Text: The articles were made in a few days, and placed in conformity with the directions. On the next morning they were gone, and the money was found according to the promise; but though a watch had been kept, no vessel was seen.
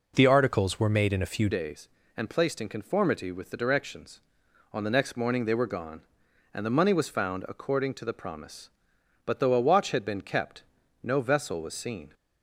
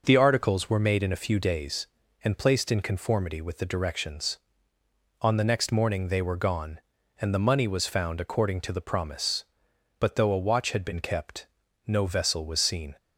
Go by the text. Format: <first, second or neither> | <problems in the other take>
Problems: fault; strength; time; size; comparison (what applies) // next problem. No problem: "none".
second | changes voice at "days"; from 1.4 s on; 10.7 s long